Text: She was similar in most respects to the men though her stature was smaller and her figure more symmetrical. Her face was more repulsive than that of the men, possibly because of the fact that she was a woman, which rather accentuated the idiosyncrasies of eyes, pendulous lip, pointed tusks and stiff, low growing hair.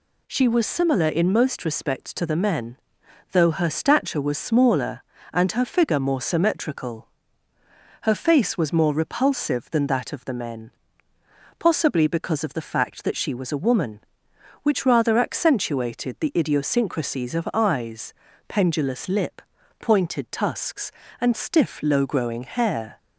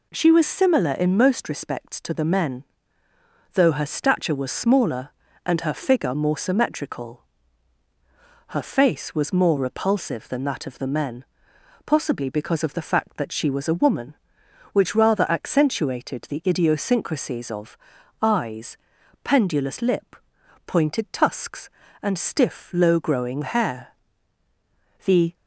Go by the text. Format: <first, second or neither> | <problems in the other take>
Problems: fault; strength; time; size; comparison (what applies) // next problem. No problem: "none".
first | pauses between "men" and "though"; noticeable; at 2.6 s; 0.90 s long; noticeable in the first // pauses between "of" and "eyes"; at 17.7 s; 0.44 s long // goes on to say "The"; slight; from 25.0 s on; 0.30 s long